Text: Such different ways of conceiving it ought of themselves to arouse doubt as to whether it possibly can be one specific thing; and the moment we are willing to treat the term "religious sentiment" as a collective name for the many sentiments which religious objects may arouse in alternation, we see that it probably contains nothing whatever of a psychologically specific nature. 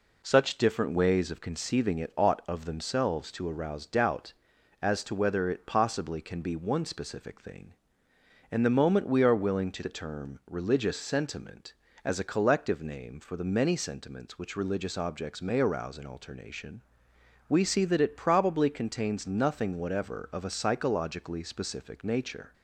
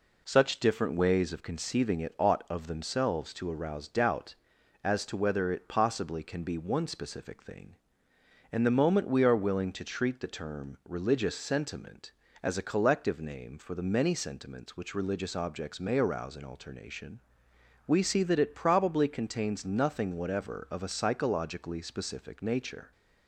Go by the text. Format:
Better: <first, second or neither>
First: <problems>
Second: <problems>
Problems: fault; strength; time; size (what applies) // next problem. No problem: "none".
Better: second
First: skips "treat"; at 9.8 s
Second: none